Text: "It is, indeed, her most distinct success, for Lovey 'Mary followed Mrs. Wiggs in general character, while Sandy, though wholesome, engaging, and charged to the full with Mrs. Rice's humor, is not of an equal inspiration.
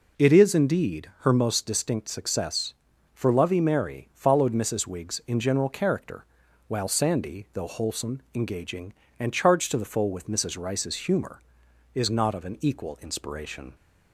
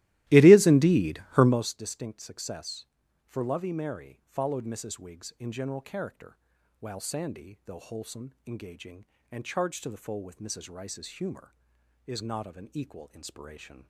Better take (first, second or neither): first